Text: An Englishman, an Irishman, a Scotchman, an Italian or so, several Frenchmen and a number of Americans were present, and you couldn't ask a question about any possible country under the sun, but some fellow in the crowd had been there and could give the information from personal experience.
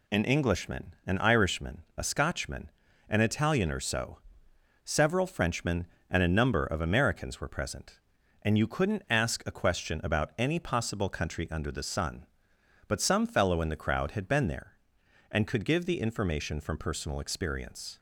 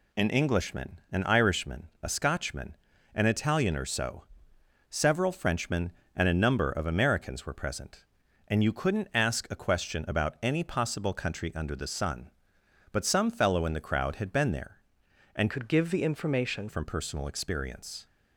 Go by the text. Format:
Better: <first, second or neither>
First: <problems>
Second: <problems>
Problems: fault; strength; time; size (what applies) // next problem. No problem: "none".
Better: first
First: none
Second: changes voice from "could" to "information"; from 15.4 to 16.6 s; 1.2 s long